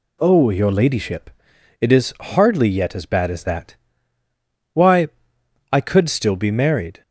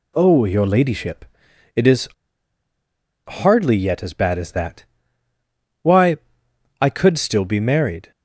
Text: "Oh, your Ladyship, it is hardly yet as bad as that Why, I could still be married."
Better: first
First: pauses between "that" and "Why"; noticeable; at 3.7 s; 0.96 s long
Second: pauses between "is" and "hardly"; at 2.0 s; 1.1 s long // pauses between "that" and "Why"; noticeable; at 4.8 s; 0.96 s long

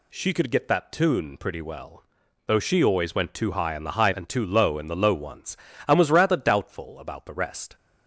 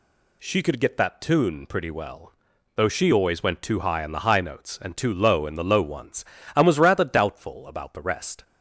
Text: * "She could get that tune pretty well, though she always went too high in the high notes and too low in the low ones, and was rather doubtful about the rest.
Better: second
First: skips "notes"; at 4.1 s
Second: none

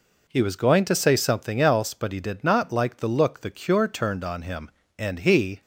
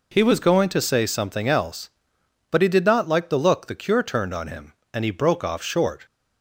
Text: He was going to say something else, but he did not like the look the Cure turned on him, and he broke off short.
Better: second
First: stops before "broke off short"; at 5.6 s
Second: none

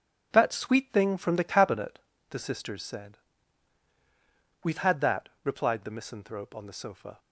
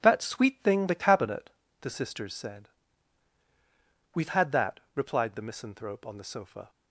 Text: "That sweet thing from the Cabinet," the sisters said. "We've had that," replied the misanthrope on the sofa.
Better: first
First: none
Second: skips "from"; at 0.8 s

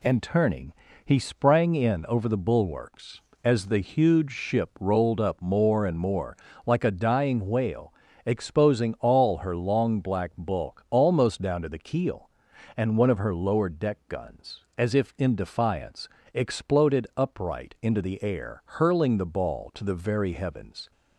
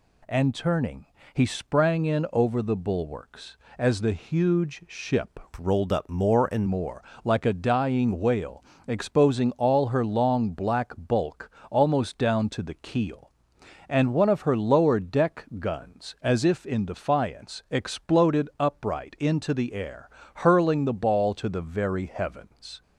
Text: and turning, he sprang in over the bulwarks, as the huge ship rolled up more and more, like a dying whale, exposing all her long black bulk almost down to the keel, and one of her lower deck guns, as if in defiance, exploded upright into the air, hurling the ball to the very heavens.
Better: first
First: none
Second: changes voice from "rolled" to "and"; from 5.5 to 6.6 s; 1.1 s long // pauses between "bulk" and "almost"; slight; at 11.4 s; 0.20 s long

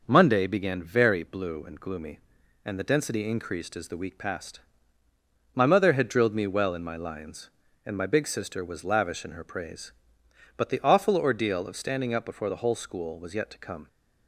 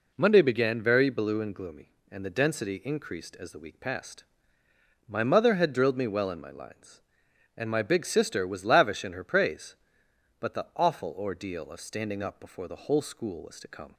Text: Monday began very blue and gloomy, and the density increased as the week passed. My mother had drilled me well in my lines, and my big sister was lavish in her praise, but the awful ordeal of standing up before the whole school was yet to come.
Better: first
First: none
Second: skips "yet"; at 13.5 s

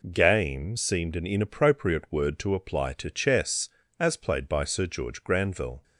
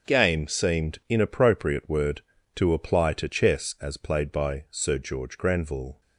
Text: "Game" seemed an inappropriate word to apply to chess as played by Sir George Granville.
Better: first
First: none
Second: starts louder than the rest; until 1.1 s; 6.5 dB // skips "an"; at 1.0 s

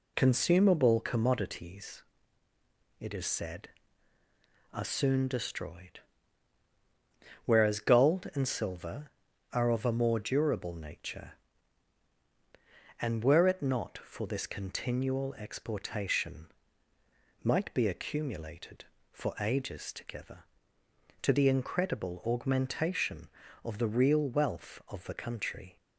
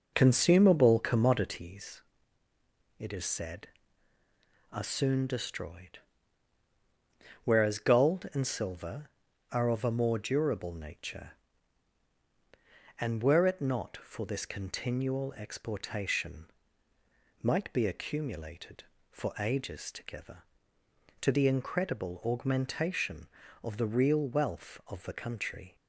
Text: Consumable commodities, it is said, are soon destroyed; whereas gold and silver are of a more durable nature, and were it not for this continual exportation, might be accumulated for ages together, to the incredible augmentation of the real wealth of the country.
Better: first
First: none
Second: starts louder than the rest; noticeable; until 1.7 s; 5 dB

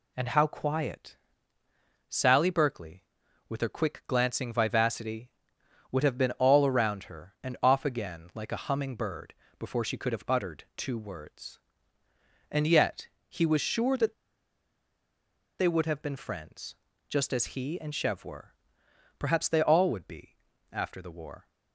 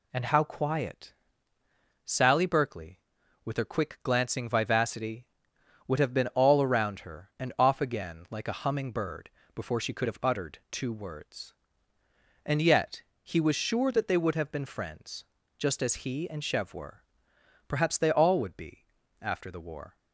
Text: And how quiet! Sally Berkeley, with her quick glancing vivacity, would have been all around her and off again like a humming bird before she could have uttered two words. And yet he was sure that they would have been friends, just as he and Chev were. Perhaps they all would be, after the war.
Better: second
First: pauses between "bird" and "before"; slight; at 9.3 s; 0.24 s long // pauses between "yet" and "he"; slight; at 13.0 s; 0.20 s long // pauses between "that" and "they"; strong; at 14.1 s; 1.4 s long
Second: pauses between "bird" and "before"; slight; at 9.2 s; 0.24 s long // pauses between "yet" and "he"; slight; at 13.0 s; 0.20 s long

